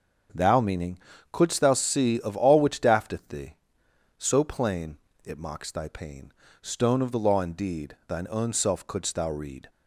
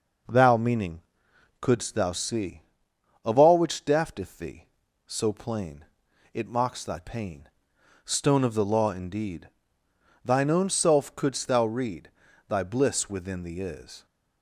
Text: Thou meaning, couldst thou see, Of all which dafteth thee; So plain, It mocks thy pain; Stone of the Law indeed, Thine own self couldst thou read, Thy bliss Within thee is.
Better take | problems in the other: second | starts louder than the rest; until 1.6 s; 6.5 dB // stops before "Thy bliss Within thee is"; at 9.7 s

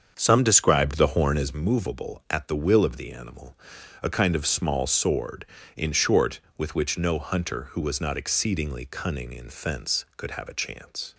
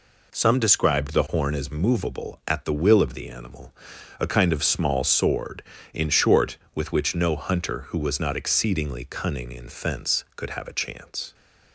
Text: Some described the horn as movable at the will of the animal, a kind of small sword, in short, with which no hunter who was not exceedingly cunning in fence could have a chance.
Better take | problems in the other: second | starts louder than the rest; until 1.6 s; 7 dB

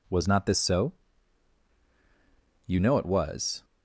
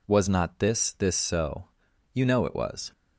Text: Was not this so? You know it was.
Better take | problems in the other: first | says "this" twice; at 0.9 s

